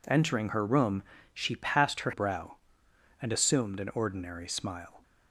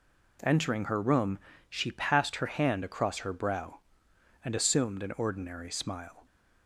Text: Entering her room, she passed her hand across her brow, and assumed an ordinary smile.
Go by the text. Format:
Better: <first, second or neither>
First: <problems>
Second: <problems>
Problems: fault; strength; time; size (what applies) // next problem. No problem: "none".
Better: second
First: skips "hand across her"; at 2.1 s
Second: none